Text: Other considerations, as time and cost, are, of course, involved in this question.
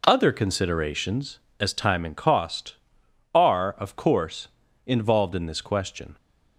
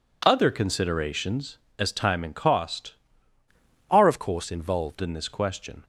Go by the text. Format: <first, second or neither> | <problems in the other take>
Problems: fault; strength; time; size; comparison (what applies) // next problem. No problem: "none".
first | changes voice from "are" to "involved"; from 3.9 to 4.9 s; 1.0 s long